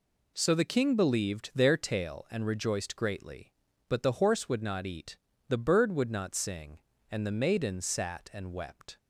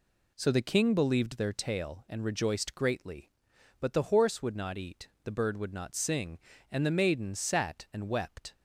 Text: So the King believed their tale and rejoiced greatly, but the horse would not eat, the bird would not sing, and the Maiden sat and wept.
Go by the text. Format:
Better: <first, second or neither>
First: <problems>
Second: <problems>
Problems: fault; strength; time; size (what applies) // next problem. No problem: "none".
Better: neither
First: none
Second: none